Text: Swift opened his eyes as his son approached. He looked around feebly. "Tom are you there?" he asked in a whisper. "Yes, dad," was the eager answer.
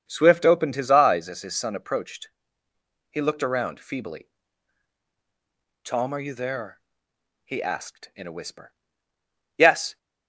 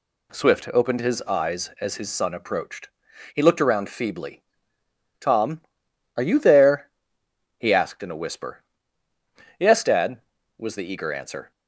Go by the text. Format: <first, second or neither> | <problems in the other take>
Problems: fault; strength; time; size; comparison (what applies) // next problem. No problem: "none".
second | starts louder than the rest; strong; until 1.0 s; 7 dB // stops before "dad was the eager answer"; at 9.9 s